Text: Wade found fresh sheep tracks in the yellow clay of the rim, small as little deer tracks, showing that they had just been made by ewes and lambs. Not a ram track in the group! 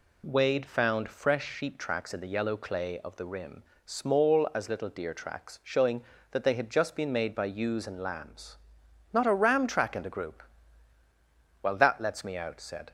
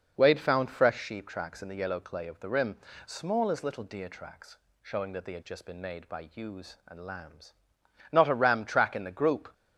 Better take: second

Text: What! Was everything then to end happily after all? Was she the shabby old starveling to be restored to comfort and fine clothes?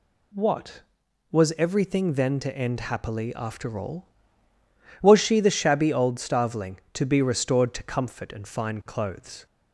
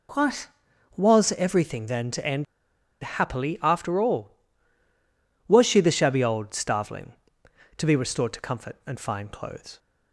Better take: first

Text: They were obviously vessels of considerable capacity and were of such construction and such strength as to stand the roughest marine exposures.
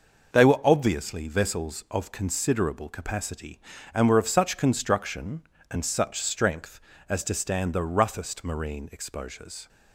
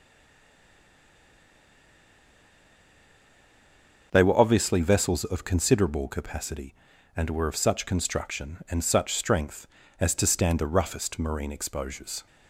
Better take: first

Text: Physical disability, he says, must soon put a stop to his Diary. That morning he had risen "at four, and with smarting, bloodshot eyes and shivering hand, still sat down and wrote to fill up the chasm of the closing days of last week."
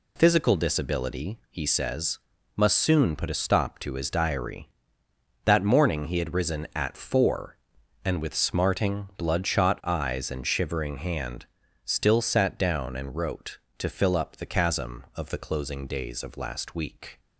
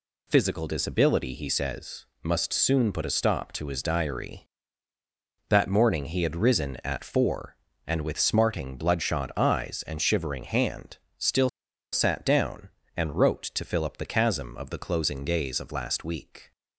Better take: first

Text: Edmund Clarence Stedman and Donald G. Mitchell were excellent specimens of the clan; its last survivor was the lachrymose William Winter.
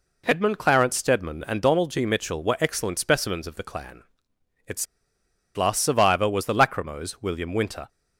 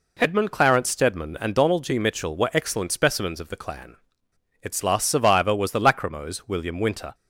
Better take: second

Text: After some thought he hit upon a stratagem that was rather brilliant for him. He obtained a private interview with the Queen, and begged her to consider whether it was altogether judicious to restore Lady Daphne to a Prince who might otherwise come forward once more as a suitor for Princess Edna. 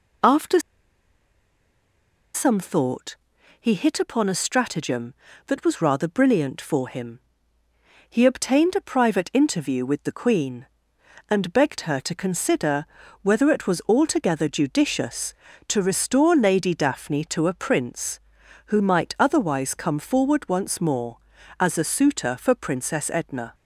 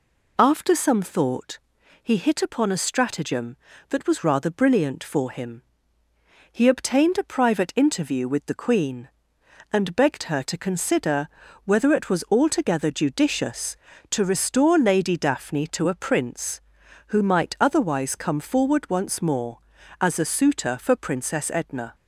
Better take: second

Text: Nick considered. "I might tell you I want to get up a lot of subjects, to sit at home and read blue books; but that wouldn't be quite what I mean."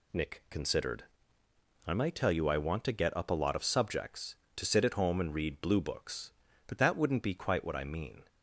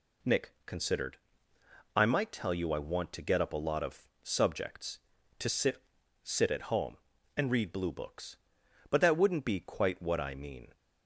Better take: first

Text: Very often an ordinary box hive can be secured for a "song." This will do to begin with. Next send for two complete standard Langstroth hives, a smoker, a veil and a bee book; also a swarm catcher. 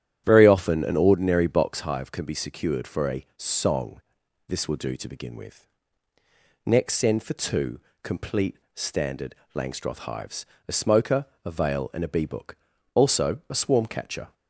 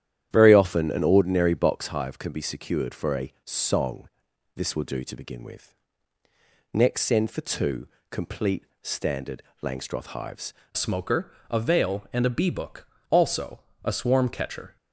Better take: first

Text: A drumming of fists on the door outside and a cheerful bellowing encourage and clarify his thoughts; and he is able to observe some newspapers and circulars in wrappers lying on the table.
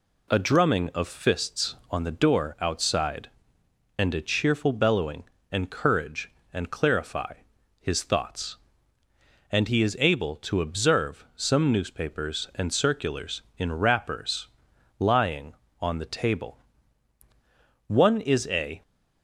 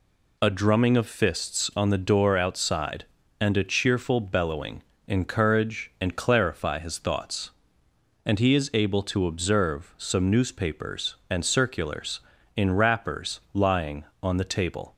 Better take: second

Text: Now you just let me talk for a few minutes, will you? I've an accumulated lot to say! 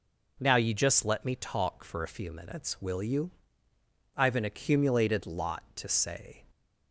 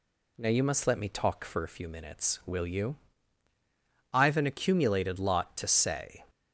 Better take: first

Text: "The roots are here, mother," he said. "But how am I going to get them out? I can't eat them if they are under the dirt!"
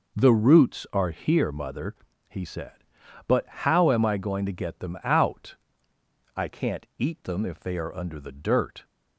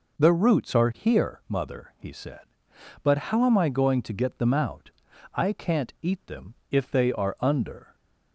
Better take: first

